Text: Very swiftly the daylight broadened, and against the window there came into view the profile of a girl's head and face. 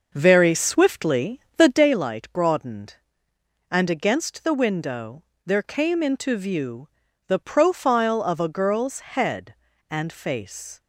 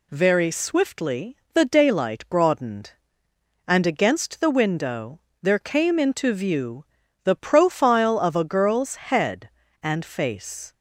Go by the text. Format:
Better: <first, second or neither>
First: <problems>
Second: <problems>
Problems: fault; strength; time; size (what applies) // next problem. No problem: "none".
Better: second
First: starts louder than the rest; noticeable; until 1.9 s; 6 dB // pauses between "swiftly" and "the"; slight; at 1.4 s; 0.16 s long // pauses between "window" and "there"; slight; at 5.2 s; 0.24 s long // pauses between "view" and "the"; at 6.8 s; 0.40 s long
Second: pauses between "swiftly" and "the"; slight; at 1.3 s; 0.16 s long // pauses between "window" and "there"; slight; at 5.1 s; 0.24 s long // pauses between "view" and "the"; at 6.8 s; 0.40 s long